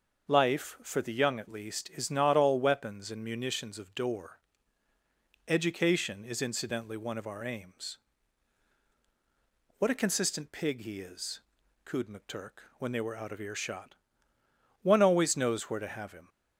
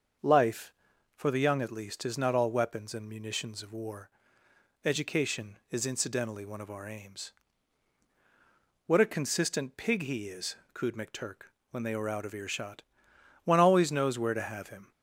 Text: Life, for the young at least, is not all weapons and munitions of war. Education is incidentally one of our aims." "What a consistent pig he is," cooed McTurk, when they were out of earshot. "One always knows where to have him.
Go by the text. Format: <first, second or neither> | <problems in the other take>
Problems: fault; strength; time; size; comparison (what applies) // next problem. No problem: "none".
second | starts louder than the rest; until 1.3 s; 6.5 dB; also in the second // says "door" for "war"; at 3.9 s